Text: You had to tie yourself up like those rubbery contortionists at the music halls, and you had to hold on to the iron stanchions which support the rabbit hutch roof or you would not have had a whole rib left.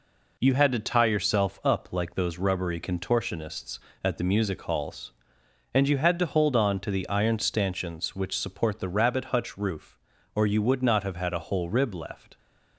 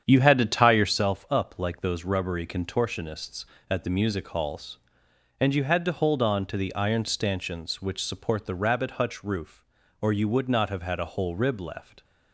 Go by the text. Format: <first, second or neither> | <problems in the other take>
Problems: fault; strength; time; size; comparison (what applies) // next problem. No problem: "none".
first | starts louder than the rest; strong; until 1.0 s; 8.5 dB